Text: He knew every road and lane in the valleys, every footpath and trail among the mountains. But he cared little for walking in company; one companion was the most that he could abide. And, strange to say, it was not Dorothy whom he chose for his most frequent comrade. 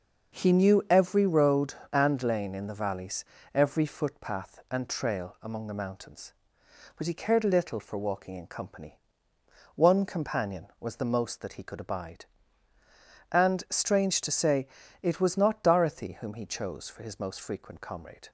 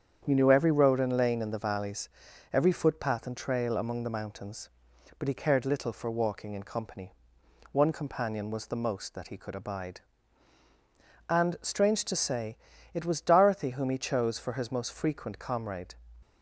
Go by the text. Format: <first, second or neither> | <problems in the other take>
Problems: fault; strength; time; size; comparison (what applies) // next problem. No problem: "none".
first | starts louder than the rest; strong; until 1.2 s; 8 dB; also in the first // skips "not"; at 13.1 s